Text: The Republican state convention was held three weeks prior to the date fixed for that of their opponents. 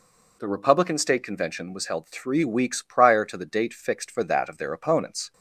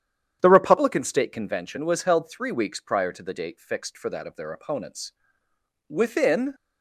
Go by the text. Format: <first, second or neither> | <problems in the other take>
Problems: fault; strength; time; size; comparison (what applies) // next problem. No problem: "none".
first | starts louder than the rest; strong; until 1.4 s; 9.5 dB // goes on to say "Within"; noticeable; from 5.8 s on; 0.66 s long